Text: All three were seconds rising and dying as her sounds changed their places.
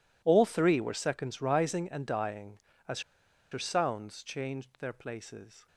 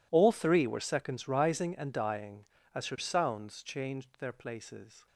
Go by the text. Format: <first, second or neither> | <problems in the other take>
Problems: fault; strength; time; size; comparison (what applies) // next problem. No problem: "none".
second | pauses between "as" and "her"; noticeable; at 2.9 s; 0.51 s long